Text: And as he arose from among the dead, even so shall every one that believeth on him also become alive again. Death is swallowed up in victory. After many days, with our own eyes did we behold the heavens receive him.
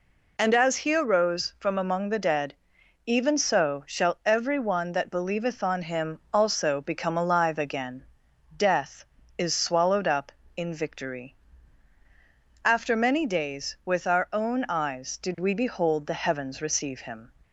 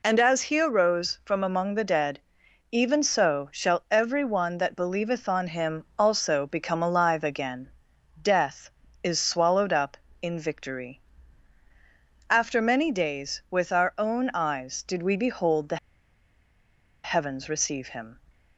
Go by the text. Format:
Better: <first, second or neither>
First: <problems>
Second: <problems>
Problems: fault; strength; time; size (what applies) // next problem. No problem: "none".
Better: first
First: none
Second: pauses between "the" and "heavens"; strong; at 15.7 s; 1.2 s long